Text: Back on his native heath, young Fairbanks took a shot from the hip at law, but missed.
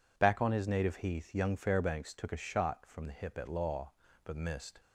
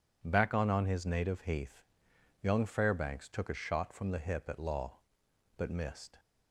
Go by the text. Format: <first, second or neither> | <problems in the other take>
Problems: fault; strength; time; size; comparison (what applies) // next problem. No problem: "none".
first | says "on" twice; at 0.6 s